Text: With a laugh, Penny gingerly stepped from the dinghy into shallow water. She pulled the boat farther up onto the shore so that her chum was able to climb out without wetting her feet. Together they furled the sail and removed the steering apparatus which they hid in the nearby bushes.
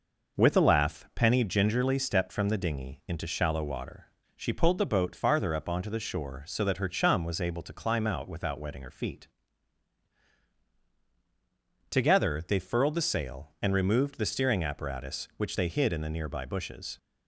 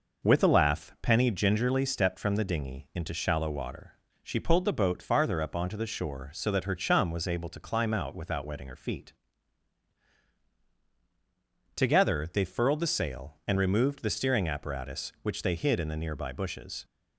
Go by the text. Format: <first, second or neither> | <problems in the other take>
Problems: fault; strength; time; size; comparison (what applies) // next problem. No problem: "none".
neither | none